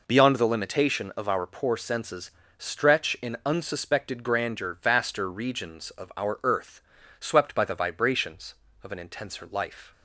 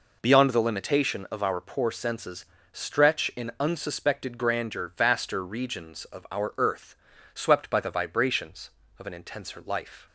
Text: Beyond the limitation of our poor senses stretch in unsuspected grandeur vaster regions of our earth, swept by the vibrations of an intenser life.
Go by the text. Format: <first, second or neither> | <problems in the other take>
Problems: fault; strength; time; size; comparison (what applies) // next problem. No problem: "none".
neither | pauses between "senses" and "stretch"; slight; the same in both